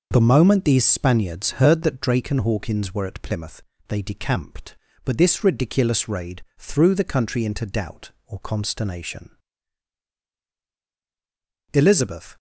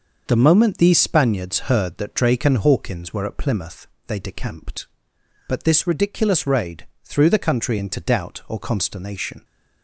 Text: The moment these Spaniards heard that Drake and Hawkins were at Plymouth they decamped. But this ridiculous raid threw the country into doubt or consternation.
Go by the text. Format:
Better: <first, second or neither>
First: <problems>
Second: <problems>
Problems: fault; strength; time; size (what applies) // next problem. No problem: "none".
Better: second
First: starts louder than the rest; noticeable; until 1.1 s; 6 dB // pauses between "Plymouth" and "they"; slight; at 3.6 s; 0.26 s long // pauses between "raid" and "threw"; slight; at 6.4 s; 0.16 s long // goes on to say "Elizabeth"; noticeable; from 11.7 s on; 0.64 s long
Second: starts louder than the rest; noticeable; until 1.2 s; 6 dB // pauses between "Plymouth" and "they"; slight; at 3.8 s; 0.20 s long // pauses between "raid" and "threw"; slight; at 6.8 s; 0.16 s long